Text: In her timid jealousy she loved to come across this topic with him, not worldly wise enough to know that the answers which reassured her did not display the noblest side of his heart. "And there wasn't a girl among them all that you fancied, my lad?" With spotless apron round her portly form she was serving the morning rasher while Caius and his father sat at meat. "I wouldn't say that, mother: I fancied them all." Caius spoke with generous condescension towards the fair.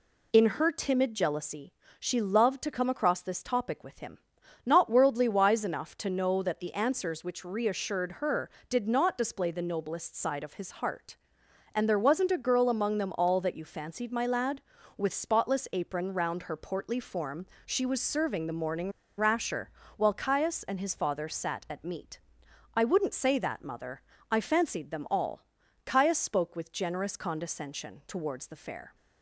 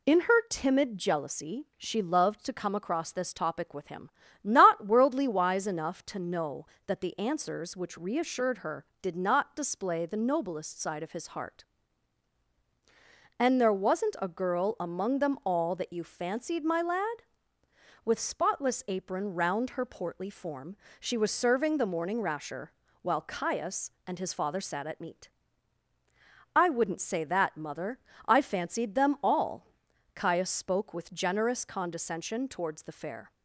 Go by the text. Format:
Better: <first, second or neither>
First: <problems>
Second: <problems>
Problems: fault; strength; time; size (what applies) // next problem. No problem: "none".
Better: second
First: pauses between "jealousy" and "she"; slight; at 1.7 s; 0.26 s long // pauses between "form" and "she"; slight; at 17.4 s; 0.22 s long // pauses between "morning" and "rasher"; slight; at 18.9 s; 0.27 s long // pauses between "rasher" and "while"; slight; at 19.6 s; 0.28 s long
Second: pauses between "form" and "she"; slight; at 20.7 s; 0.24 s long // pauses between "rasher" and "while"; slight; at 22.7 s; 0.26 s long